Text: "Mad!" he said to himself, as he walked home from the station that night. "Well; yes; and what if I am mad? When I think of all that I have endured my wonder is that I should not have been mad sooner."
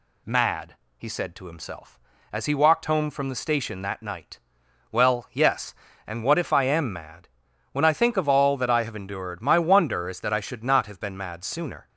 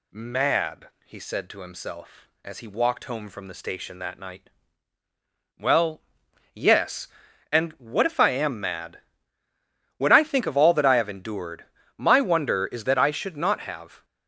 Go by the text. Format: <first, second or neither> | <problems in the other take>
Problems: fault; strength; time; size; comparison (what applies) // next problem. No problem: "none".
first | pauses between "endured" and "my"; slight; at 11.6 s; 0.32 s long // stops before "been mad sooner"; at 14.0 s